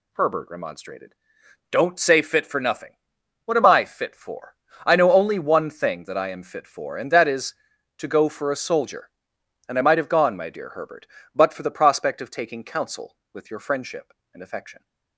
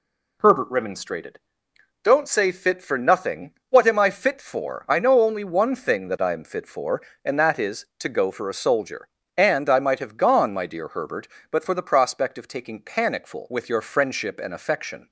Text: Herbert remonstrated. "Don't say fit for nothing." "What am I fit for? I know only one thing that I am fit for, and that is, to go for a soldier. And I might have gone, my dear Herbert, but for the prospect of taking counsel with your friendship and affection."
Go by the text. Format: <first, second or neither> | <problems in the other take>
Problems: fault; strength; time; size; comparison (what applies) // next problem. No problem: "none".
first | says "panicful" for "counsel"; at 12.8 s